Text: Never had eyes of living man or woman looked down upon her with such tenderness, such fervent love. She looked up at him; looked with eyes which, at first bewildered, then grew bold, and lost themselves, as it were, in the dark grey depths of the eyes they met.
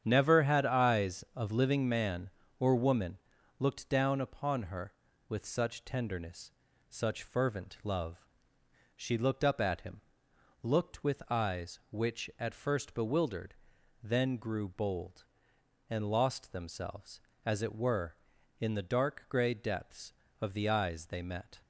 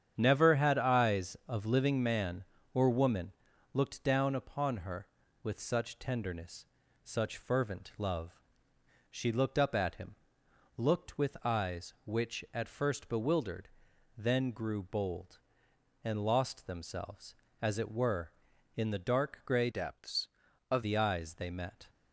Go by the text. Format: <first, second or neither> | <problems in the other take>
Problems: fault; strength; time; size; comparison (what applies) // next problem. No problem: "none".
first | starts louder than the rest; strong; until 1.1 s; 8.5 dB; strong in the first // pauses between "woman" and "looked"; at 3.3 s; 0.42 s long; also in the first // changes voice from "depths" to "of"; from 19.7 to 20.8 s; 1.1 s long